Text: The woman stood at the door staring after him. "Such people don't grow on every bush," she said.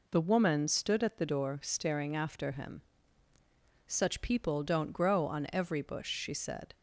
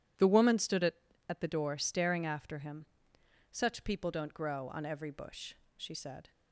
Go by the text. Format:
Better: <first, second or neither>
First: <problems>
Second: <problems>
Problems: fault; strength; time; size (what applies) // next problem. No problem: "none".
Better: first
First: none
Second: says "at" twice; at 1.2 s